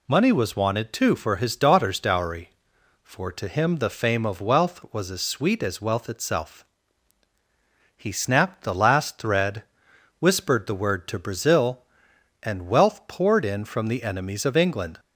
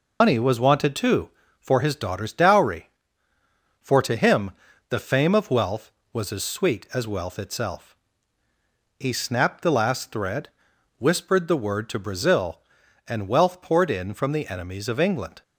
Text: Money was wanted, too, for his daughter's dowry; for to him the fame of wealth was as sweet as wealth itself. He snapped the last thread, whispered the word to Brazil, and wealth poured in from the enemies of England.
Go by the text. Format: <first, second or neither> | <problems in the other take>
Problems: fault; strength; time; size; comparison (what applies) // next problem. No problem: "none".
first | loses the start of "Money"; at 0.2 s; 135 ms // pauses between "him" and "the"; slight; at 4.5 s; 0.36 s long